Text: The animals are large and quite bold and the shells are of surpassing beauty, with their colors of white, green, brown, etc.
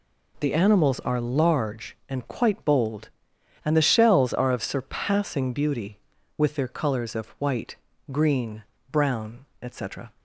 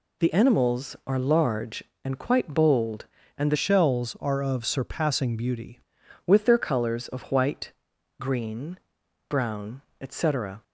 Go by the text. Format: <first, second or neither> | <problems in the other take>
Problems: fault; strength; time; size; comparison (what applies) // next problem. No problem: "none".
first | changes voice from "shells" to "beauty"; from 3.5 to 5.8 s; 2.3 s long